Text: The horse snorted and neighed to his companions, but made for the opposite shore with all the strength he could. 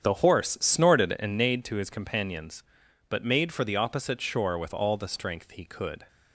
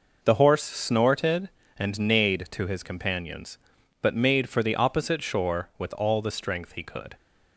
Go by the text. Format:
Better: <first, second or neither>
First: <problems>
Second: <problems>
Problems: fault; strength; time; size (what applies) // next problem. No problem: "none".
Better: second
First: starts louder than the rest; strong; until 1.5 s; 8 dB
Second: none